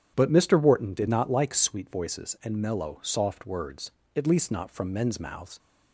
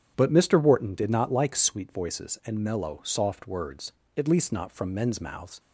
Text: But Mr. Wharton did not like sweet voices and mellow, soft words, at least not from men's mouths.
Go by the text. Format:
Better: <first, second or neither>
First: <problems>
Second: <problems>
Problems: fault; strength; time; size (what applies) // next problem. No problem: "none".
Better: neither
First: starts louder than the rest; strong; until 1.1 s; 9.5 dB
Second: starts louder than the rest; strong; until 1.1 s; 9.5 dB